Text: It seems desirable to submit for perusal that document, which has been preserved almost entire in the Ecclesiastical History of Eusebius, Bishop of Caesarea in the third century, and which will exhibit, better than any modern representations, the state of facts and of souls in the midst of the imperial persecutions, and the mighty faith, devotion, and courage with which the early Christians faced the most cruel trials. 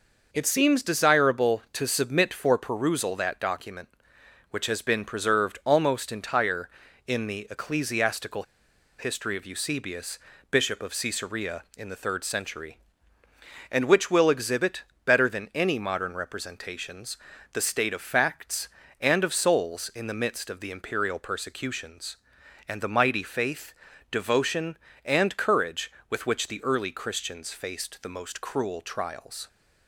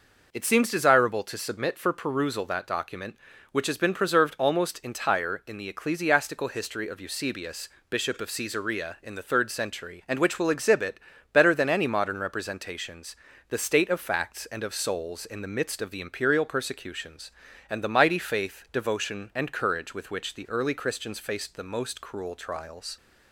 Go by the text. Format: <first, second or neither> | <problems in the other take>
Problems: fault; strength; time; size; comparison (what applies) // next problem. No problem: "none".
second | pauses between "Ecclesiastical" and "History"; noticeable; at 8.4 s; 0.54 s long